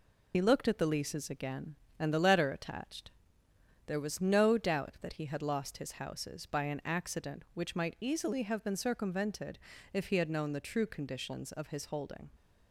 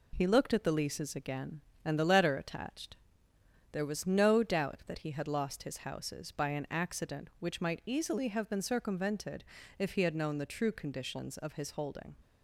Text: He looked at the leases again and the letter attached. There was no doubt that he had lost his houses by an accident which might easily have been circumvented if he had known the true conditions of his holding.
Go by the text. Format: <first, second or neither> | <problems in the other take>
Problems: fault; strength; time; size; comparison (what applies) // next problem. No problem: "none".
second | loses the start of "He"; at 0.3 s; 70 ms // pauses between "circumvented" and "if"; slight; at 9.5 s; 0.34 s long; slight in the second